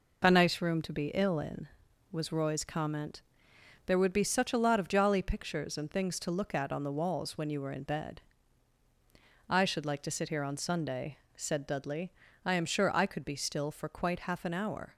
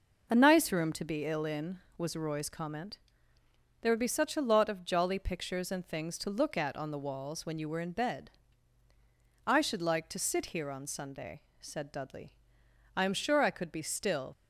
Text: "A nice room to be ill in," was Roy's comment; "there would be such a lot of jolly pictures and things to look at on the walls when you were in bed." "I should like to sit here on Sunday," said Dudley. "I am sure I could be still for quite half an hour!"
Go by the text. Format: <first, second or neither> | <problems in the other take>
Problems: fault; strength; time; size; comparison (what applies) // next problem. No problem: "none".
first | stops before "for quite half an hour"; at 14.3 s